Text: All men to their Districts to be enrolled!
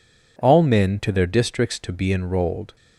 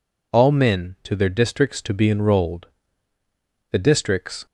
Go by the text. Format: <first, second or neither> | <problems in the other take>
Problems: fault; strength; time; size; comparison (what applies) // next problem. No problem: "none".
first | goes on to say "The Districts"; noticeable; from 3.7 s on; 0.74 s long